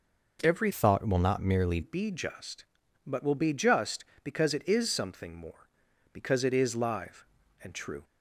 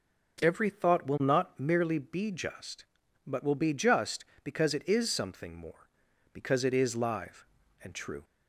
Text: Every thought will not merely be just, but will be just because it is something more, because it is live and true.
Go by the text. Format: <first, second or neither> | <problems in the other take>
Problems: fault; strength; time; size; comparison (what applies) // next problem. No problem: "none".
second | changes voice from "thought" to "merely"; from 0.7 to 1.8 s; 1.1 s long